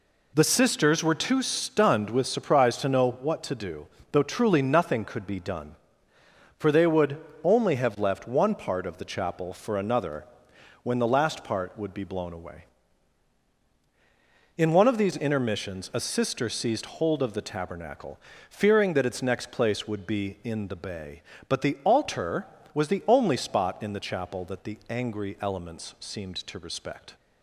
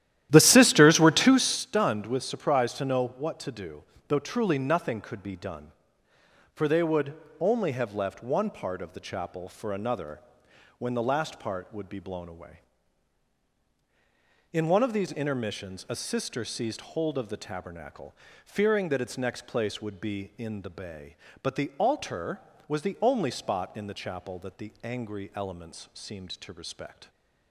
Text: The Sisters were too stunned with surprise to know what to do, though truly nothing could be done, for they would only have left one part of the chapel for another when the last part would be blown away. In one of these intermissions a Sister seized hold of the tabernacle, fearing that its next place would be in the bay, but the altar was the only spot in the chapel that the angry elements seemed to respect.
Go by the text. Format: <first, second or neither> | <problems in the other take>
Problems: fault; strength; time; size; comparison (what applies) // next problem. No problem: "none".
first | starts louder than the rest; strong; until 1.7 s; 13 dB // pauses between "would" and "only"; slight; at 7.1 s; 0.26 s long; slight in the first // pauses between "another" and "when"; noticeable; at 10.2 s; 0.58 s long; noticeable in the first